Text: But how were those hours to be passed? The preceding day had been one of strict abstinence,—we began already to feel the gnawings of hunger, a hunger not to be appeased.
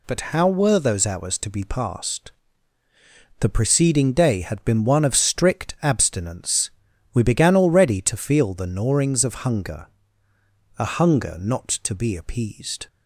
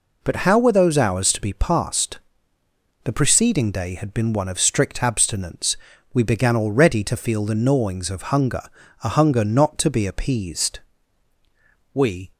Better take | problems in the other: first | goes on to say "We"; slight; from 11.9 s on; 0.38 s long

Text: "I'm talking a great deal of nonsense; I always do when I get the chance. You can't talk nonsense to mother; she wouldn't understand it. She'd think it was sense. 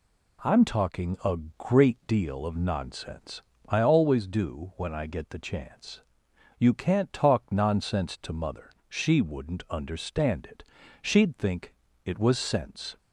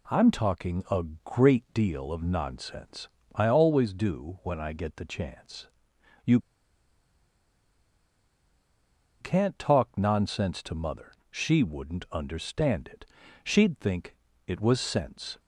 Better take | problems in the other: first | pauses between "a" and "great"; slight; at 1.0 s; 0.22 s long; slight in the first // pauses between "You" and "can't"; strong; at 6.3 s; 2.8 s long // pauses between "think" and "it"; slight; at 14.1 s; 0.30 s long; slight in the first

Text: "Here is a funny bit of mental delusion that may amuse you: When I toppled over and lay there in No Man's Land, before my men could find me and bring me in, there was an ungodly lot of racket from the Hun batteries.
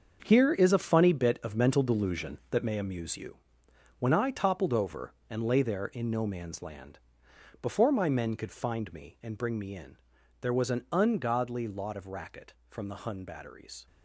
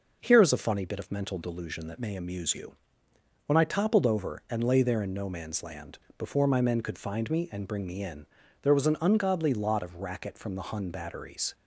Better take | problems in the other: second | gets quieter; strong; throughout; 10 dB

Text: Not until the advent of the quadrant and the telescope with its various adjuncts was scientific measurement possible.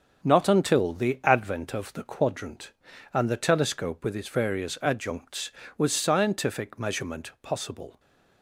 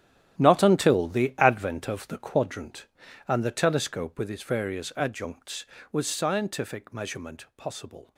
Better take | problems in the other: first | gets quieter; strong; throughout; 13.5 dB // starts louder than the rest; strong; until 1.4 s; 11 dB; also in the first

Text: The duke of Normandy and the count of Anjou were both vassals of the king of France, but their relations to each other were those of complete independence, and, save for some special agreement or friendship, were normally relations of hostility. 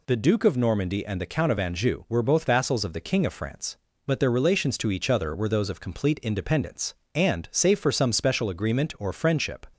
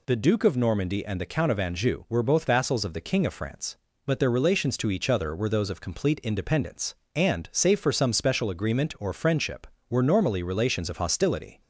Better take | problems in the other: second | stops before "were normally relations of hostility"; at 9.7 s

